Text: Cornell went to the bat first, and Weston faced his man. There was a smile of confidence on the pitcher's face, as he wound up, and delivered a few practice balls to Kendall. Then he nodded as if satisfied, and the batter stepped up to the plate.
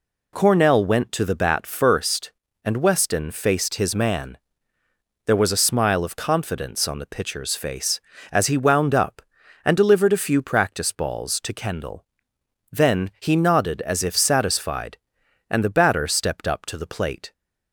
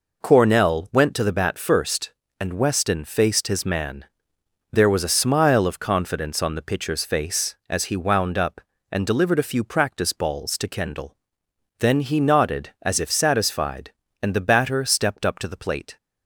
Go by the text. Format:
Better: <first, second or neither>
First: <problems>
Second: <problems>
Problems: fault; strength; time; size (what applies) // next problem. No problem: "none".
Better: neither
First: none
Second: none